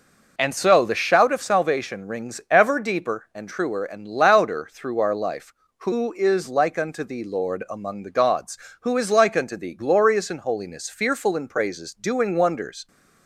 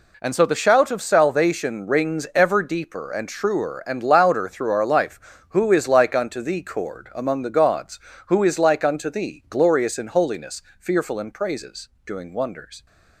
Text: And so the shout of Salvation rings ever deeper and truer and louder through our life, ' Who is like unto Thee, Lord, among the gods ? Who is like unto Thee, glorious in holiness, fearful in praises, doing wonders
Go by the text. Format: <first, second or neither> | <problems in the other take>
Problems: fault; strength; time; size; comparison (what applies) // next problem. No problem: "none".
first | says "Cord" for "Lord"; at 6.6 s